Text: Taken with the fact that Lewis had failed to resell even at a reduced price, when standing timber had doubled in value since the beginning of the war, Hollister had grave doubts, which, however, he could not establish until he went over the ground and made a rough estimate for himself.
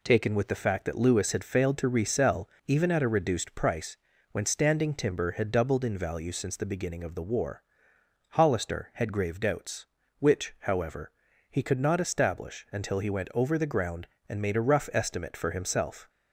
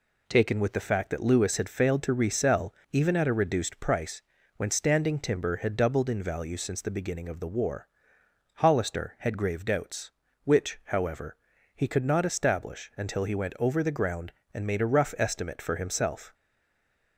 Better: first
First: pauses between "resell" and "even"; slight; at 2.4 s; 0.18 s long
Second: pauses between "resell" and "even"; slight; at 2.7 s; 0.18 s long // stays silent after the last word; slight; from 16.3 s on; 0.8 s long

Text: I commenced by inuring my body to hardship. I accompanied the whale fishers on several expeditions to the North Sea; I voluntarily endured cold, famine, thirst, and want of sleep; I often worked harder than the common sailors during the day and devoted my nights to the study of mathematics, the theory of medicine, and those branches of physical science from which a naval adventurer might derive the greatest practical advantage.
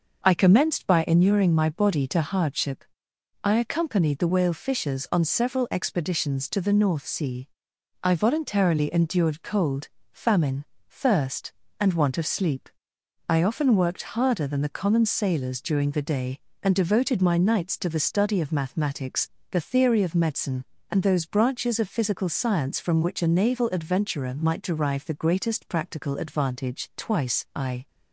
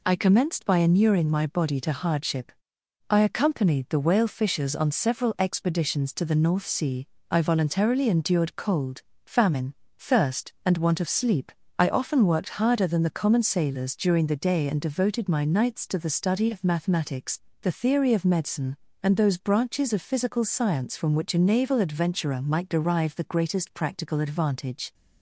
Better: second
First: goes on to say "Twice I"; noticeable; from 26.9 s on; 0.92 s long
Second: none

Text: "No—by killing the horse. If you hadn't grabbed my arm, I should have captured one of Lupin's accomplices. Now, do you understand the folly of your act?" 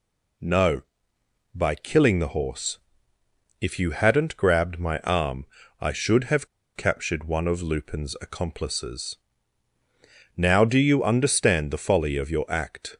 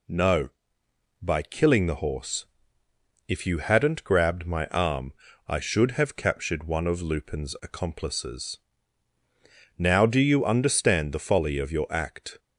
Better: second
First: pauses between "have" and "captured"; slight; at 6.4 s; 0.29 s long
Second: none

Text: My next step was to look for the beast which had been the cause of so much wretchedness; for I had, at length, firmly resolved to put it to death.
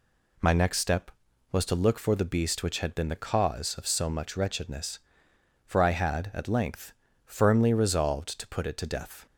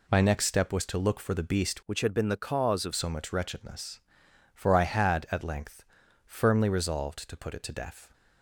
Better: first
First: none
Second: changes voice from "which" to "of"; from 1.8 to 2.9 s; 1.1 s long

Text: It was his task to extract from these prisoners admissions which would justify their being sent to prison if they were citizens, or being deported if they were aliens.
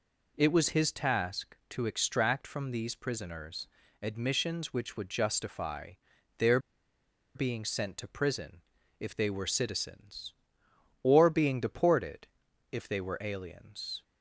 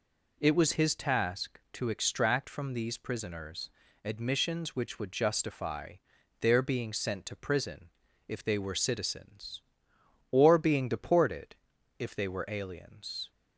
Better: second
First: pauses between "prisoners" and "admissions"; slight; at 3.6 s; 0.34 s long // pauses between "justify" and "their"; noticeable; at 5.9 s; 0.46 s long // pauses between "their" and "being"; noticeable; at 6.5 s; 0.76 s long // pauses between "prison" and "if"; at 8.6 s; 0.38 s long // pauses between "deported" and "if"; at 12.2 s; 0.44 s long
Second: pauses between "prisoners" and "admissions"; slight; at 3.7 s; 0.34 s long // pauses between "justify" and "their"; noticeable; at 5.9 s; 0.46 s long // pauses between "prison" and "if"; at 7.8 s; 0.38 s long // pauses between "deported" and "if"; at 11.5 s; 0.42 s long

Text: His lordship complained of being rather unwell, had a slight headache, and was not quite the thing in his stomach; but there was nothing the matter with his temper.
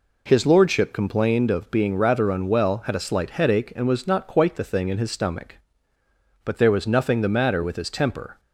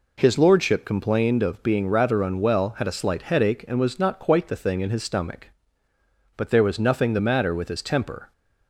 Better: neither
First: none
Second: none

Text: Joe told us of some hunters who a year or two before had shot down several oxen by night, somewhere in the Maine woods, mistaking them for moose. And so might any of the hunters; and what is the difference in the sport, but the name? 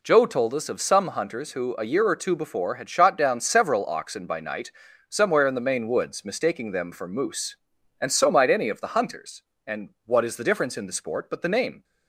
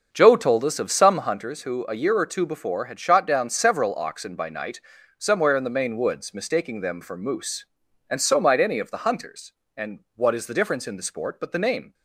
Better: first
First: pauses between "and" and "what"; slight; at 9.8 s; 0.16 s long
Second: starts louder than the rest; until 1.5 s; 6.5 dB // pauses between "and" and "what"; slight; at 9.9 s; 0.16 s long

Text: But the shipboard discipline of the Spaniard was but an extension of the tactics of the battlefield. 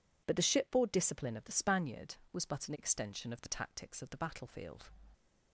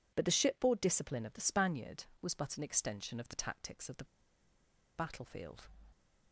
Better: first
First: none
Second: pauses between "the" and "battlefield"; noticeable; at 4.0 s; 0.92 s long

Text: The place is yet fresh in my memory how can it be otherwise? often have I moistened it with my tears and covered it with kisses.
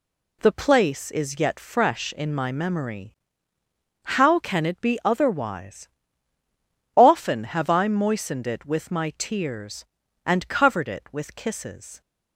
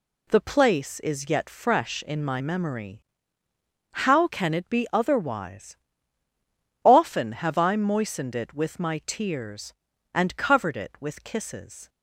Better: neither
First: pauses between "memory" and "how"; noticeable; at 3.1 s; 0.98 s long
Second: pauses between "memory" and "how"; noticeable; at 3.0 s; 0.98 s long

